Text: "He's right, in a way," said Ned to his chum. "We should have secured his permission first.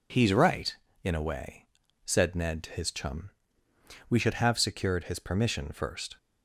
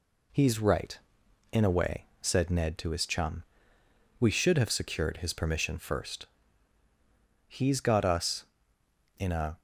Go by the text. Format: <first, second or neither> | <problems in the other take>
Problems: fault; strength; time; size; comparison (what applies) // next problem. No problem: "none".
first | goes on to say "He's got us in a"; strong; from 7.4 s on; 2.1 s long